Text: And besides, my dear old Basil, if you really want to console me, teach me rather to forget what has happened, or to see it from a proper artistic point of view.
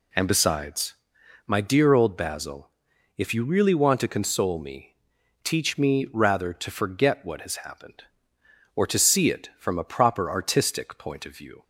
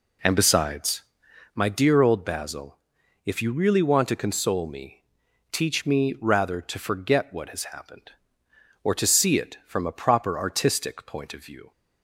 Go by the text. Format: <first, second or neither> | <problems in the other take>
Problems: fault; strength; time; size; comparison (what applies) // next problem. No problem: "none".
first | starts louder than the rest; slight; until 1.5 s; 3 dB